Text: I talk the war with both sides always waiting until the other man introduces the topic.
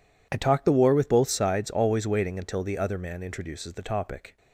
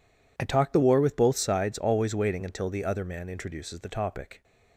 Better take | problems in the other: neither | none

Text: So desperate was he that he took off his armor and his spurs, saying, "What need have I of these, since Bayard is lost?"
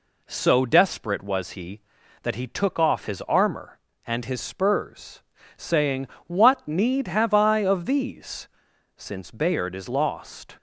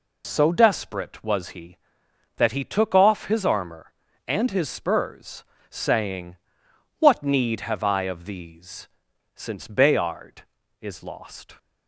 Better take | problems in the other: neither | none

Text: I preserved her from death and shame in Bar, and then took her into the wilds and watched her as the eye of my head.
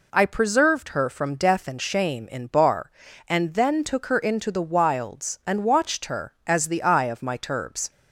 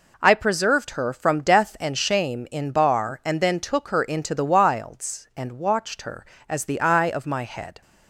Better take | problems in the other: second | says "turbs" for "head"; at 7.3 s

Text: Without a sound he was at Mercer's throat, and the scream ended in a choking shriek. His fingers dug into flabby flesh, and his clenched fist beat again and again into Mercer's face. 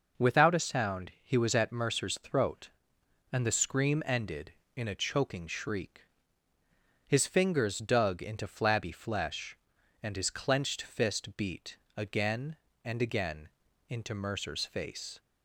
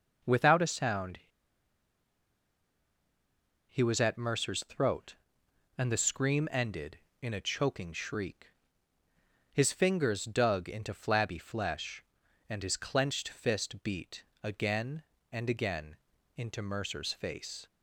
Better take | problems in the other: first | pauses between "sound" and "he"; strong; at 1.1 s; 2.5 s long // pauses between "beat" and "again"; slight; at 14.2 s; 0.20 s long; slight in the first // pauses between "again" and "into"; at 15.9 s; 0.40 s long; also in the first

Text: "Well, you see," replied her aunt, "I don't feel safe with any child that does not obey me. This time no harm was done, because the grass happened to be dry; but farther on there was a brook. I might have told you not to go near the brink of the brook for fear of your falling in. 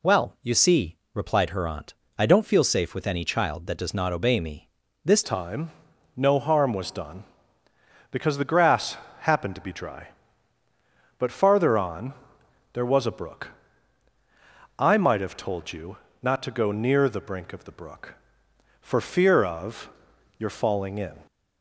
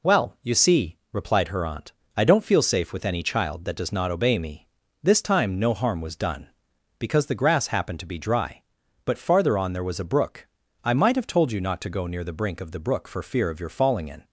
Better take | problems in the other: second | changes voice at "time"; from 5.2 s on; 16.0 s long // pauses between "time" and "no"; at 5.7 s; 0.44 s long // pauses between "grass" and "happened"; slight; at 8.9 s; 0.26 s long // pauses between "on" and "there"; noticeable; at 12.1 s; 0.60 s long // pauses between "you" and "not"; slight; at 15.9 s; 0.24 s long // pauses between "of" and "your"; noticeable; at 19.8 s; 0.48 s long

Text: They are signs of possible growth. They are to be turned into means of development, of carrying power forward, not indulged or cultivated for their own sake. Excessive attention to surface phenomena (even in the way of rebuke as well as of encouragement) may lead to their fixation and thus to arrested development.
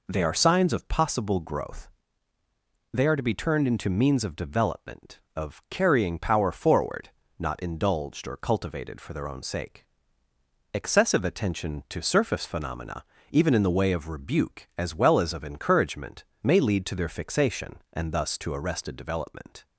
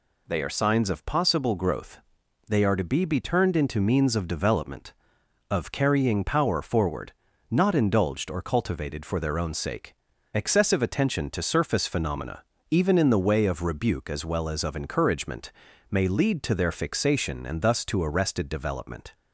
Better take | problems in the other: first | says "be" twice; at 3.0 s

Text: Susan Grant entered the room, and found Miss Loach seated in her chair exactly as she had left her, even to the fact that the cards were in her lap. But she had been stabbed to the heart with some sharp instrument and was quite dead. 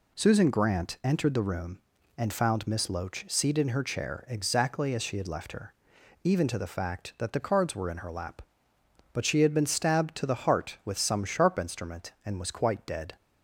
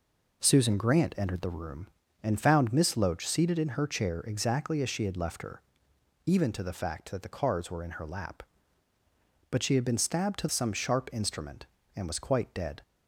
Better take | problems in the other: first | skips "the heart with"; at 10.4 s

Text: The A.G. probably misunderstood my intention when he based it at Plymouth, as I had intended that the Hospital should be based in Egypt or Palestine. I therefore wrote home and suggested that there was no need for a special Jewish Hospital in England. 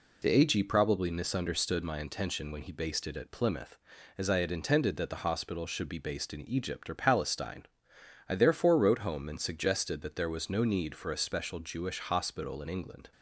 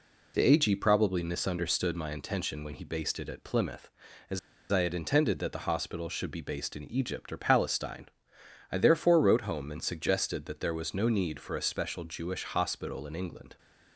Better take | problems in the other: first | pauses between "as" and "I"; slight; at 4.3 s; 0.32 s long

